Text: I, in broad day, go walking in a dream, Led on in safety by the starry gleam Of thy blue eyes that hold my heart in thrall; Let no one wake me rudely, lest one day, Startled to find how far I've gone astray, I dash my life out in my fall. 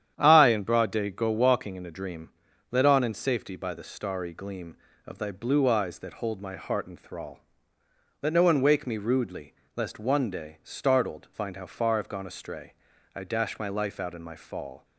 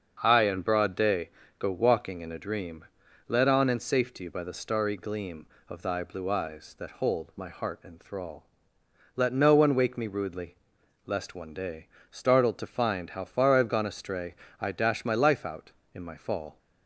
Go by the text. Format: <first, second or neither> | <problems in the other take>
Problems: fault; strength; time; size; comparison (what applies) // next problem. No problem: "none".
second | starts louder than the rest; strong; until 1.1 s; 9.5 dB; also in the second // skips "to"; at 11.2 s